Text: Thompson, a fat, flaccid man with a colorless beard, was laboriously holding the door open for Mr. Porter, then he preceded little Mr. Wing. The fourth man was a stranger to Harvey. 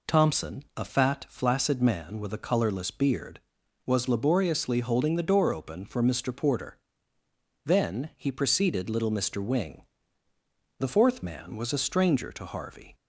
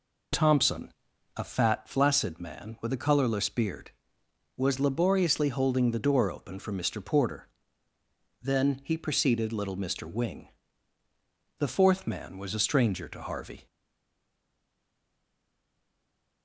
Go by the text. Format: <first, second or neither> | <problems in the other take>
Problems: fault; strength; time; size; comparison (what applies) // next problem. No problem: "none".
first | stays silent after the last word; strong; from 13.6 s on; 2.8 s long